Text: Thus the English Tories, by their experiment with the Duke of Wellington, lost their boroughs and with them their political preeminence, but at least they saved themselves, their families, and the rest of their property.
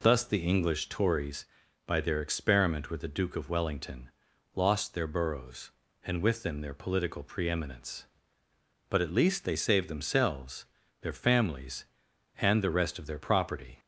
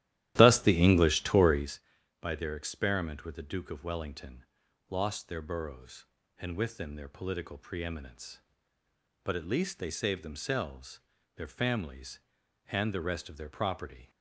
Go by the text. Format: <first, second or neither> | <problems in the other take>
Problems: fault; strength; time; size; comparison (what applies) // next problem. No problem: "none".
first | starts louder than the rest; strong; until 1.9 s; 13.5 dB